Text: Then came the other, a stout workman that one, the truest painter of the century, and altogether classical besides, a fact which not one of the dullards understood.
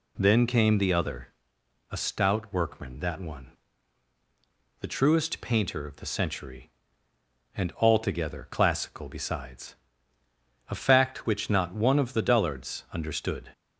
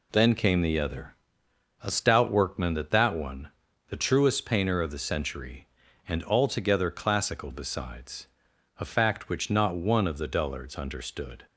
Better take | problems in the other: first | says "that" twice; at 2.9 s

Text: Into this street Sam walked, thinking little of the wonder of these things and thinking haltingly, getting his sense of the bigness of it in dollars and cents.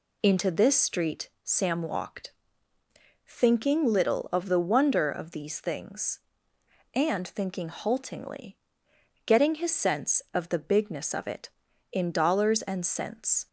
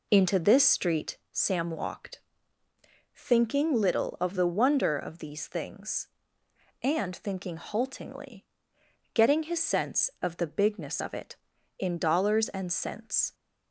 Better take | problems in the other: first | starts louder than the rest; until 1.3 s; 3.5 dB // pauses between "street" and "Sam"; slight; at 1.1 s; 0.16 s long; slight in the first

